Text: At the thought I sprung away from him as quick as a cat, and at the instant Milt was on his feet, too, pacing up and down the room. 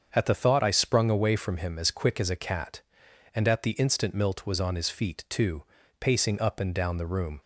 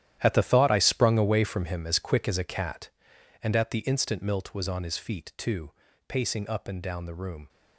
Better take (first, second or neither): first